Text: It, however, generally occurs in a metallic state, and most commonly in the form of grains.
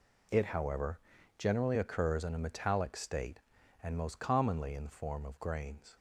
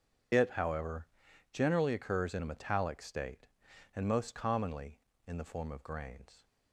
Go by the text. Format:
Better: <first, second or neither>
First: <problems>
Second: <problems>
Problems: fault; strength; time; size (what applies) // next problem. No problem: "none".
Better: first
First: none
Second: loses the start of "It"; at 0.3 s; 50 ms